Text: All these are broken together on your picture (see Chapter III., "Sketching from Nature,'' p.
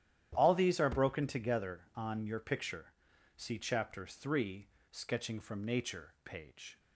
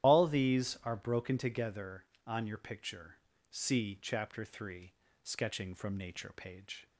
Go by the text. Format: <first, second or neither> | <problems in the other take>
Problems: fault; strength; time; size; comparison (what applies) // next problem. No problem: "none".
first | loses the start of "All"; at 0.0 s; 70 ms // starts louder than the rest; strong; until 1.1 s; 11.5 dB; strong in the first